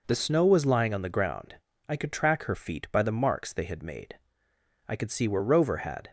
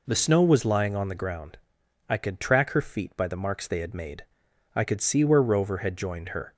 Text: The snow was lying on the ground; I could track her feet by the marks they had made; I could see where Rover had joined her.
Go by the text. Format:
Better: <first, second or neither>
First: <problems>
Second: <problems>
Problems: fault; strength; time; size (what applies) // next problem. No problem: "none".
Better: second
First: stops before "joined her"; at 6.0 s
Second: none